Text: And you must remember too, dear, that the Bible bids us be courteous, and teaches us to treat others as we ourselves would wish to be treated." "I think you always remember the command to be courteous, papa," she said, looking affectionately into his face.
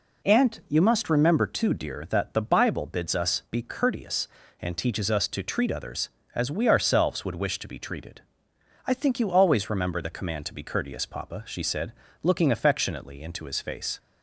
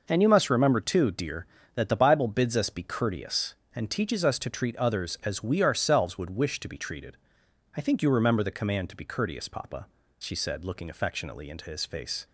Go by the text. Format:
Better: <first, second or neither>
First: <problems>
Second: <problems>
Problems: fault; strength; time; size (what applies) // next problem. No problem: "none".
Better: first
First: none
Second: skips "always"; at 8.0 s